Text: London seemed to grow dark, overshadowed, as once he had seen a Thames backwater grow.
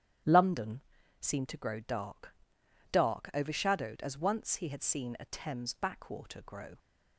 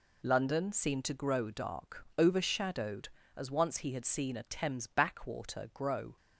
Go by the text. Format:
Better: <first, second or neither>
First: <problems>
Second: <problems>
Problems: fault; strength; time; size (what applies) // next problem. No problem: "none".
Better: second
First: starts louder than the rest; strong; until 1.6 s; 11.5 dB // pauses between "London" and "seemed"; at 0.7 s; 0.40 s long // says "dark" twice; at 2.9 s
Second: none